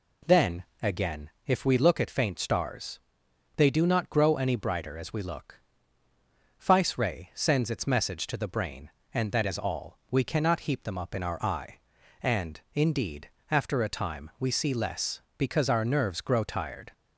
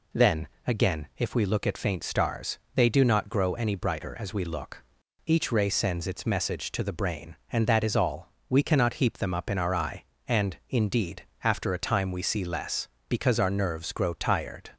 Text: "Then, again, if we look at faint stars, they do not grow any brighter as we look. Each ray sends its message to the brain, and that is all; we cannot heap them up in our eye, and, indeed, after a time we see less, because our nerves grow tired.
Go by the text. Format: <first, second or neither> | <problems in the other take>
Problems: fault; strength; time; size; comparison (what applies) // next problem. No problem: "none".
second | says "Fice" for "Each"; at 6.5 s